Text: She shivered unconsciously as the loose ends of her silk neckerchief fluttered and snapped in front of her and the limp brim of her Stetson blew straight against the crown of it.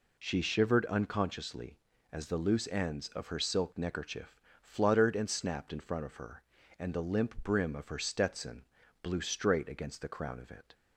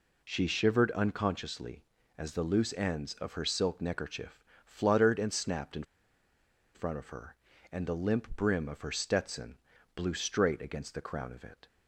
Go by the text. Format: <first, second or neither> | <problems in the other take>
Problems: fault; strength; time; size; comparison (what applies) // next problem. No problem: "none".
first | pauses between "neckerchief" and "fluttered"; slight; at 4.4 s; 0.24 s long; slight in the first // pauses between "in" and "front"; noticeable; at 5.8 s; 0.91 s long // pauses between "Stetson" and "blew"; slight; at 9.5 s; 0.36 s long; slight in the first